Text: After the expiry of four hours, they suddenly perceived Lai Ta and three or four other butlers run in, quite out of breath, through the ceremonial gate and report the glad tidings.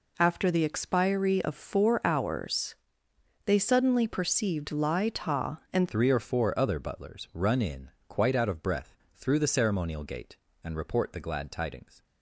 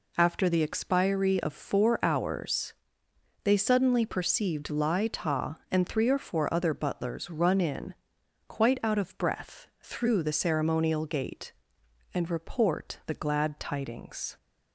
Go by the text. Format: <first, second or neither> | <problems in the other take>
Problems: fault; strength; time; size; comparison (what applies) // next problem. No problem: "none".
second | changes voice at "three"; from 5.8 s on; 6.2 s long